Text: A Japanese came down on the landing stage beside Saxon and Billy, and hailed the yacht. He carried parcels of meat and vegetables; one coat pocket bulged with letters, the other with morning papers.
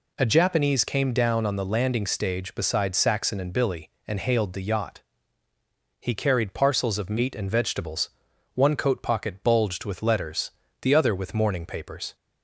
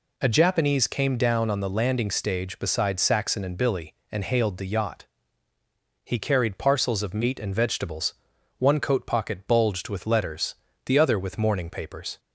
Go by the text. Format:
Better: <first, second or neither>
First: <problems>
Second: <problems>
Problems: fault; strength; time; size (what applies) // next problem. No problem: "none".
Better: neither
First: none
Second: none